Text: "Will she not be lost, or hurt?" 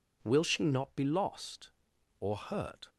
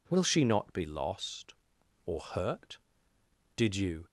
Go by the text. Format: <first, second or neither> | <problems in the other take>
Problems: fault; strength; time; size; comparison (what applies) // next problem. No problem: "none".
first | goes on to say "Did you"; from 3.5 s on; 0.50 s long